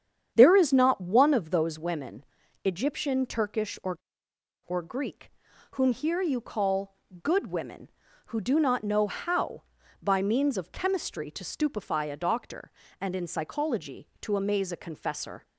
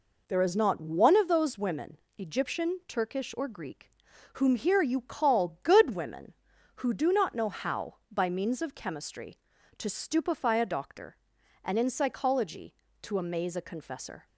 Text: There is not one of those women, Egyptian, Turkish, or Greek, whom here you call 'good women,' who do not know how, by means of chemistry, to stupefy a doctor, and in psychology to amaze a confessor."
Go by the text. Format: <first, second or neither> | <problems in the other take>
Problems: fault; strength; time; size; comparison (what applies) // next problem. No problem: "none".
second | starts louder than the rest; strong; until 1.3 s; 8.5 dB // says "or" twice; at 4.6 s // pauses between "call" and "good"; slight; at 6.9 s; 0.28 s long